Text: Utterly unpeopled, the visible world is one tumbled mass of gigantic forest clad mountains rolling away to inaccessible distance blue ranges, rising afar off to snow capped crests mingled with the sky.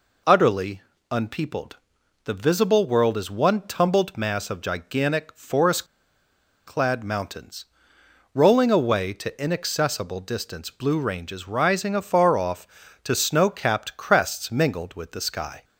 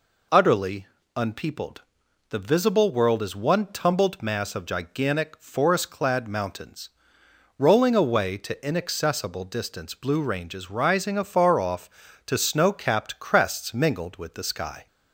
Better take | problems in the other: second | pauses between "Utterly" and "unpeopled"; slight; at 0.7 s; 0.32 s long; slight in the second // pauses between "forest" and "clad"; noticeable; at 5.8 s; 0.81 s long // pauses between "mountains" and "rolling"; noticeable; at 7.6 s; 0.68 s long; noticeable in the second

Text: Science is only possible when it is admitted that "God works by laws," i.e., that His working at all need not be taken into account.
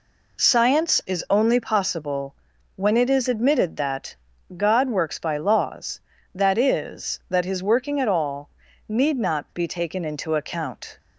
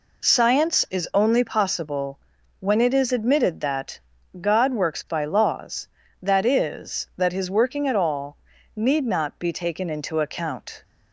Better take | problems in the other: neither | pauses between "possible" and "when"; the same in both // pauses between "that" and "God"; the same in both // pauses between "all" and "need"; the same in both

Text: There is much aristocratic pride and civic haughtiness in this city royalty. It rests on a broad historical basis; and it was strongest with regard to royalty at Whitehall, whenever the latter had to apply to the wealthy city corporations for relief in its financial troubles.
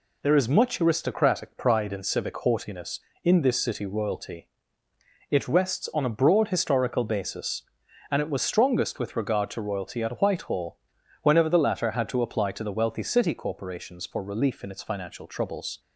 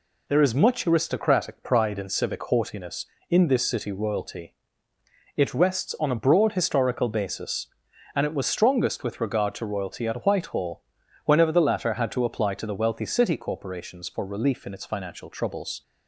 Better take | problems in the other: neither | none

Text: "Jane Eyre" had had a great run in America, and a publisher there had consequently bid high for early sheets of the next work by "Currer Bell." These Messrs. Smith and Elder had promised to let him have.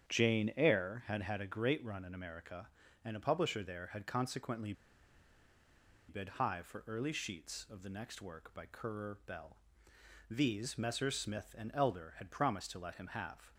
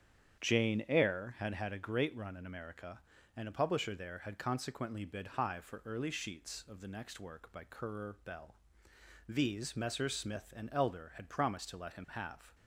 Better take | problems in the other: second | starts louder than the rest; strong; until 1.1 s; 8.5 dB; strong in the second // pauses between "consequently" and "bid"; strong; at 4.7 s; 1.3 s long

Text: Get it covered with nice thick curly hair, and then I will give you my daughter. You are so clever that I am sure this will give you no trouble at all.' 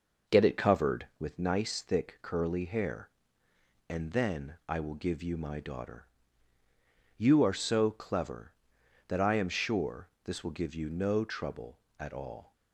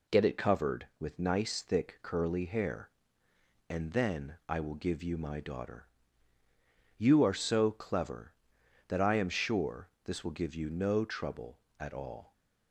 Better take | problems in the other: second | starts louder than the rest; noticeable; until 1.3 s; 5.5 dB // pauses between "sure" and "this"; slight; at 10.0 s; 0.16 s long; slight in the second

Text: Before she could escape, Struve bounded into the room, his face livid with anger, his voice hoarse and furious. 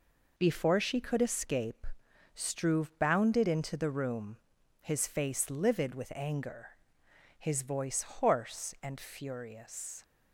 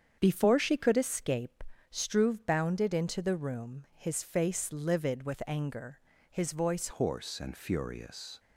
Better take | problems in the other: first | starts louder than the rest; strong; until 1.2 s; 8 dB // changes voice at "hoarse"; from 6.8 s on; 1.5 s long

